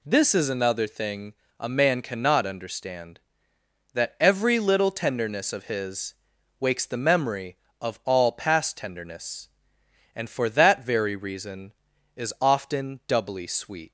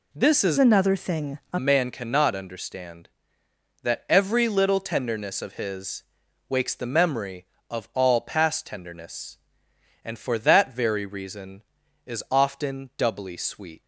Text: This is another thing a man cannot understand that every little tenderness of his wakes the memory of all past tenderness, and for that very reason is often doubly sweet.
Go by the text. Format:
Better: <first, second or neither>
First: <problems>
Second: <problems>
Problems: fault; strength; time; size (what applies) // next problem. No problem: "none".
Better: first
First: pauses between "thing" and "a"; slight; at 1.3 s; 0.24 s long // pauses between "his" and "wakes"; at 6.1 s; 0.44 s long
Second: changes voice from "another" to "a"; from 0.5 to 1.5 s; 1.0 s long // pauses between "thing" and "a"; slight; at 1.3 s; 0.16 s long // pauses between "his" and "wakes"; at 6.0 s; 0.44 s long